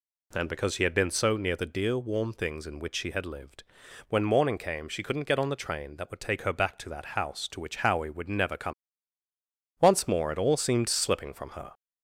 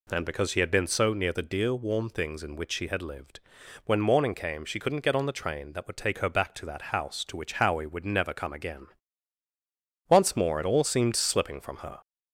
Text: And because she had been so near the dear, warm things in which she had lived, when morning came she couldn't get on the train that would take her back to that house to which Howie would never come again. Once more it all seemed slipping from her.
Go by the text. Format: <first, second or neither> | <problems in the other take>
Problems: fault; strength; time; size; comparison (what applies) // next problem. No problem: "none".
second | skips "again"; at 9.2 s